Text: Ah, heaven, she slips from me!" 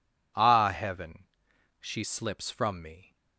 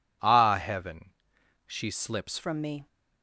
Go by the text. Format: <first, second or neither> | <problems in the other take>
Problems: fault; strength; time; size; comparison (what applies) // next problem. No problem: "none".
first | changes voice at "from"; from 2.4 s on; 0.4 s long